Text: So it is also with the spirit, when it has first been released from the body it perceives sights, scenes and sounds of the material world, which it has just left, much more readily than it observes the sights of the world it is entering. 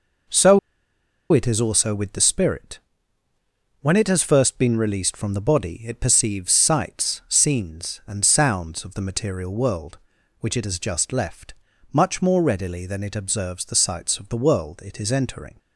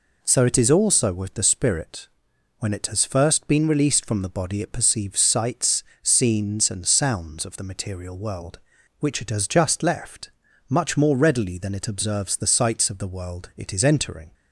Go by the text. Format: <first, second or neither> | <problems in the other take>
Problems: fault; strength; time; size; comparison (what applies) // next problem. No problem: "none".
second | pauses between "So" and "it"; noticeable; at 0.5 s; 0.73 s long